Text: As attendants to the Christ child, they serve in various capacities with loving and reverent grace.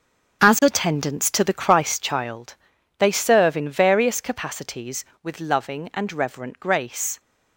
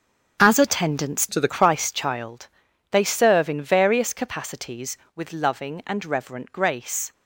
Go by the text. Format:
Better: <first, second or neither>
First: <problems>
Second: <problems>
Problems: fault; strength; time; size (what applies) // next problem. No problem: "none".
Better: first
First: starts louder than the rest; strong; until 1.5 s; 7 dB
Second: starts louder than the rest; strong; until 1.4 s; 7.5 dB // changes voice from "to" to "the"; from 1.2 to 1.4 s; 0.2 s long